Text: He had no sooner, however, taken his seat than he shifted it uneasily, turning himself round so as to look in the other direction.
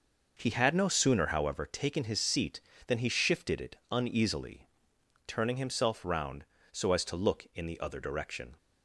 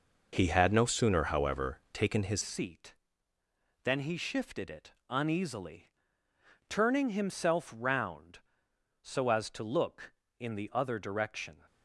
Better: first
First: none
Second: changes voice at "seat"; from 2.4 s on; 9.2 s long // pauses between "it" and "uneasily"; slight; at 4.9 s; 0.18 s long

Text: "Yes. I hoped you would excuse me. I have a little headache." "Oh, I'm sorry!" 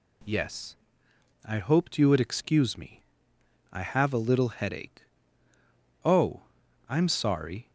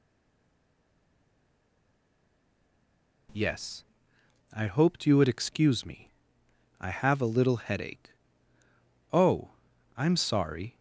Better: first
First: none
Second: stays silent before the first word; strong; until 3.2 s; 3.2 s long

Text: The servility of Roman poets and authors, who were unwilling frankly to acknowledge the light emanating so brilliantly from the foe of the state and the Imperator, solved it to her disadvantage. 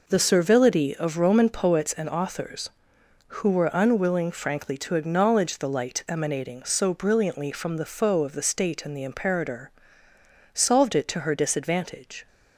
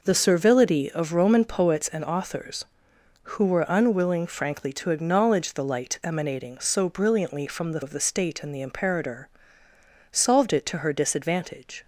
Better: first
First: none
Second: skips "foe"; at 7.8 s

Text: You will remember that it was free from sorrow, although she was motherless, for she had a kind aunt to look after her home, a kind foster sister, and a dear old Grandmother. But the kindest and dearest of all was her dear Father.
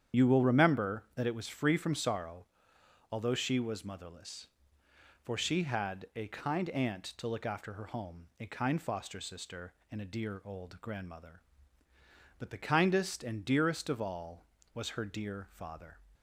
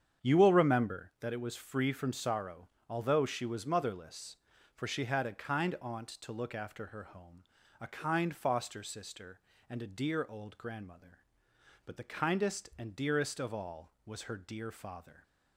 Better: second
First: loses the start of "You"; at 0.1 s; 65 ms // starts louder than the rest; strong; until 1.2 s; 9 dB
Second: starts louder than the rest; strong; until 1.3 s; 8 dB

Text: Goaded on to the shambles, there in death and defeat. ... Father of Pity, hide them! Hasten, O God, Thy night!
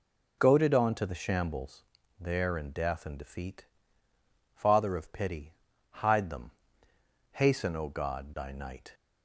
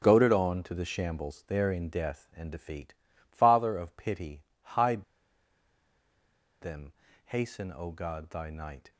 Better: first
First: none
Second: pauses between "hide" and "them"; strong; at 5.0 s; 1.5 s long

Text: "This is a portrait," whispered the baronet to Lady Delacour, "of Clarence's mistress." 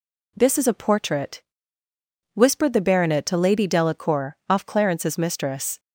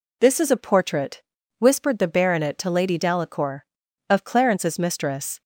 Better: second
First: says "off" for "of"; at 4.4 s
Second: none

